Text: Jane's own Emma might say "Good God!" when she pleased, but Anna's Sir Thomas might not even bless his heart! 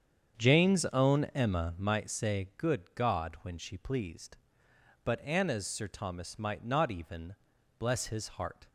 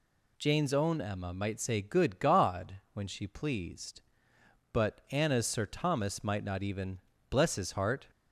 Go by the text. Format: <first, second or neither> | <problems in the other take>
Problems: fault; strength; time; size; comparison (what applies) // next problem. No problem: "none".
second | starts louder than the rest; strong; until 2.1 s; 7.5 dB // pauses between "even" and "bless"; at 7.3 s; 0.44 s long; slight in the second